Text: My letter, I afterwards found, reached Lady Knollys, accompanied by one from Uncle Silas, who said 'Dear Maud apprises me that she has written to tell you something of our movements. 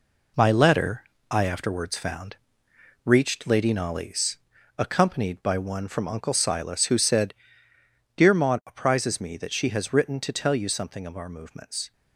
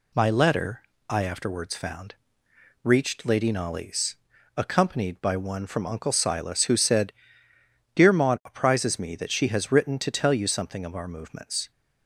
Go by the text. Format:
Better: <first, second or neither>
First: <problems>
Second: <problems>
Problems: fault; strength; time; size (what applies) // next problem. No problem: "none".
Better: second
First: gets quieter; strong; throughout; 8 dB // pauses between "said" and "Dear"; noticeable; at 7.3 s; 0.82 s long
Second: pauses between "said" and "Dear"; noticeable; at 7.1 s; 0.82 s long